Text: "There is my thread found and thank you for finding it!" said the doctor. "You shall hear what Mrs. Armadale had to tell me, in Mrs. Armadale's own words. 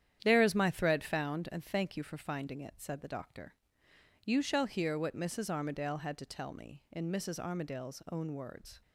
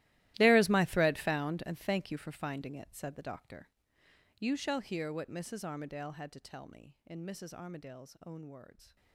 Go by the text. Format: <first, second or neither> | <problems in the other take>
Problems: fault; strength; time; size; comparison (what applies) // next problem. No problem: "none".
first | gets quieter; strong; throughout; 18.5 dB // starts louder than the rest; strong; until 1.3 s; 16 dB; strong in the first